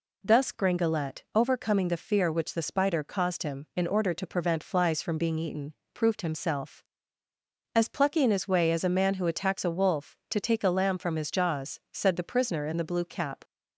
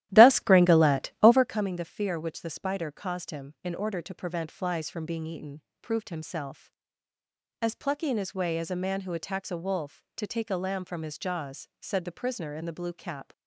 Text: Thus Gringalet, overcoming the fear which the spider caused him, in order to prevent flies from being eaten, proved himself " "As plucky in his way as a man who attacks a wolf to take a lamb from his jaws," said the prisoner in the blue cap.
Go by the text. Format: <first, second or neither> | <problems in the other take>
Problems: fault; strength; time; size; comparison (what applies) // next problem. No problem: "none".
first | starts louder than the rest; strong; until 1.6 s; 14 dB